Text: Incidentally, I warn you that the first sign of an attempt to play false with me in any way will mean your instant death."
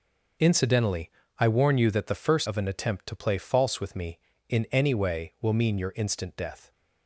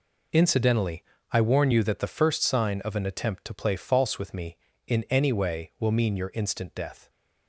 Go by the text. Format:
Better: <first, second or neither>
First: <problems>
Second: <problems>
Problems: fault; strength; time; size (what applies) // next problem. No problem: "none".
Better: second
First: skips "sign"; at 2.4 s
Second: none